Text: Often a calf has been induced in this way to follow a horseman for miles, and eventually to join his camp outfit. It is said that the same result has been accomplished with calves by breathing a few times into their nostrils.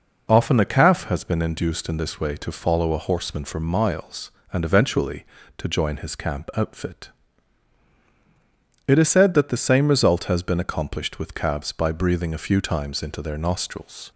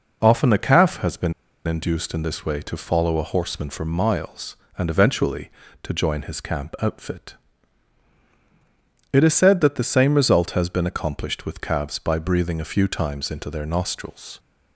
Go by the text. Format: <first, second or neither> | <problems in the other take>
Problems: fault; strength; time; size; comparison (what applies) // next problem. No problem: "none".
first | pauses between "been" and "induced"; slight; at 1.3 s; 0.33 s long